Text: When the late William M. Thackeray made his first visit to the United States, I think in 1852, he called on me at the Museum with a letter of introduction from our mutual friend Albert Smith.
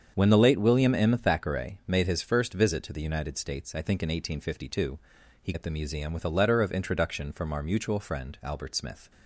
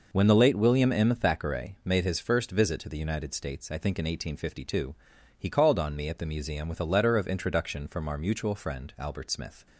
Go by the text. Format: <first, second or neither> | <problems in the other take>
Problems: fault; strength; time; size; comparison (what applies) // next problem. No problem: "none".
second | starts louder than the rest; strong; until 1.1 s; 7.5 dB // skips "called on me"; at 5.5 s